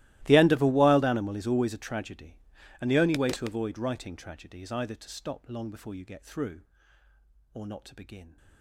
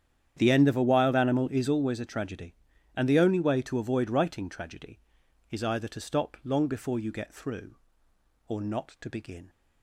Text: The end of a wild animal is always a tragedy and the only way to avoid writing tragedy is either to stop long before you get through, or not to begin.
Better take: second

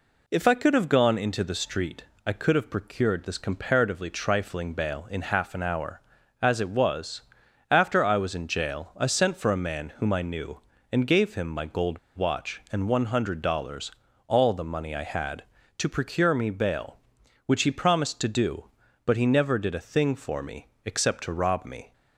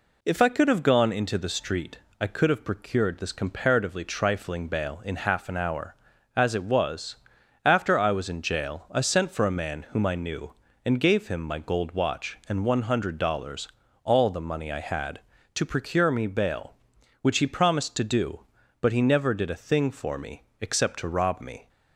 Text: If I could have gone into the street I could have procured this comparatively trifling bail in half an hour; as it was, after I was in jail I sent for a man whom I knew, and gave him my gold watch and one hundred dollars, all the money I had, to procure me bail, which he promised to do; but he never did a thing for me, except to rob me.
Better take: second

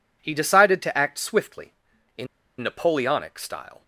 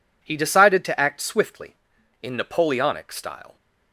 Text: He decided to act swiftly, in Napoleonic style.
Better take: second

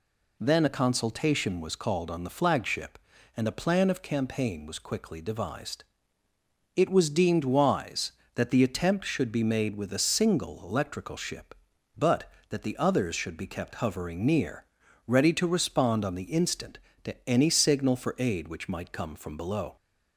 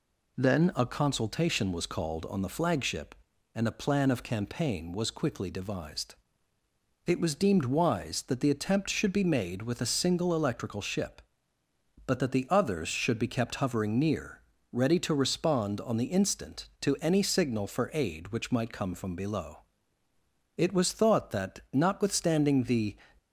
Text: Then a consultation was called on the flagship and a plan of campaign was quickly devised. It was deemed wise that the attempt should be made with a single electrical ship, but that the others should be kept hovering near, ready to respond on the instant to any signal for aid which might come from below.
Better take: first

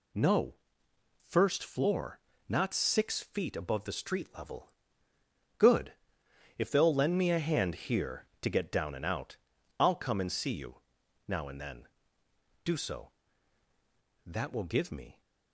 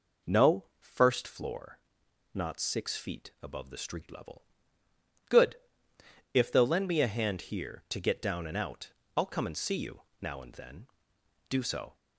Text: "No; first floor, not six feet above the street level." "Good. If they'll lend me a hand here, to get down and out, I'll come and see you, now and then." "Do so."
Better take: second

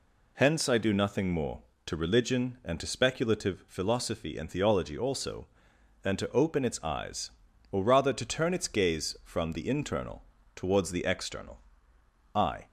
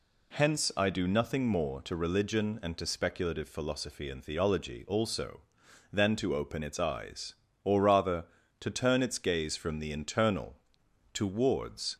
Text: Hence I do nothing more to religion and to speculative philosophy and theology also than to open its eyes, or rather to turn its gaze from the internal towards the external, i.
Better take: first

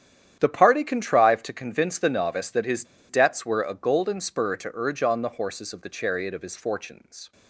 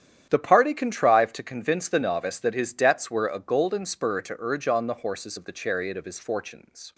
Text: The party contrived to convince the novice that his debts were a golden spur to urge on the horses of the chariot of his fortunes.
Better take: second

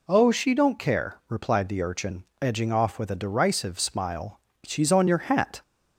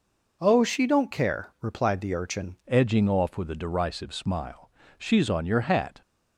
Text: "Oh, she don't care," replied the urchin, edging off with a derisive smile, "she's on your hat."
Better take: first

